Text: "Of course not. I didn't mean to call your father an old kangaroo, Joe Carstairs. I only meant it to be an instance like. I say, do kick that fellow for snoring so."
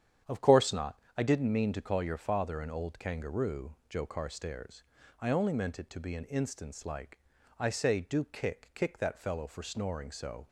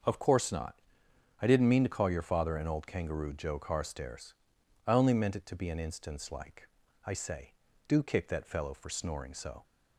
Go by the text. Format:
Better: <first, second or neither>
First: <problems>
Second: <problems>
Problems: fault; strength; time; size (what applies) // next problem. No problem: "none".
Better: second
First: starts louder than the rest; strong; until 1.4 s; 9 dB // says "kick" twice; at 8.7 s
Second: starts louder than the rest; until 1.7 s; 6.5 dB